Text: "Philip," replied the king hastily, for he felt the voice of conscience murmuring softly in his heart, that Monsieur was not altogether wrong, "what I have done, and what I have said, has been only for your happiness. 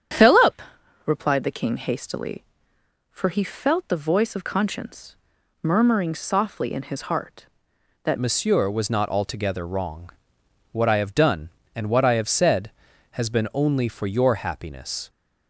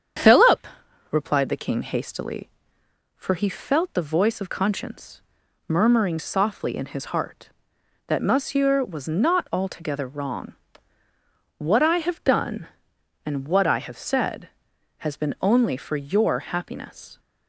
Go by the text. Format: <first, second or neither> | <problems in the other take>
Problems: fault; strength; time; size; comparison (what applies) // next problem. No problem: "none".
second | starts louder than the rest; strong; until 1.5 s; 8.5 dB; strong in the second // pauses between "conscience" and "murmuring"; noticeable; at 5.1 s; 0.46 s long; noticeable in the second // changes voice at "Monsieur"; from 8.1 s on; 6.9 s long